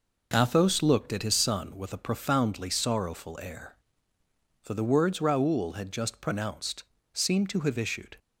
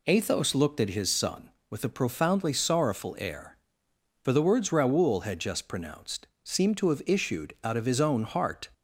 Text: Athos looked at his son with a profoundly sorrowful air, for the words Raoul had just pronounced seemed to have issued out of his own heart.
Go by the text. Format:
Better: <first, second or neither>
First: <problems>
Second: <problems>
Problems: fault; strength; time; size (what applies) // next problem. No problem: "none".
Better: second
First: pauses between "pronounced" and "seemed"; slight; at 6.8 s; 0.28 s long // stops before "out of his own heart"; at 8.1 s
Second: pauses between "pronounced" and "seemed"; slight; at 6.2 s; 0.18 s long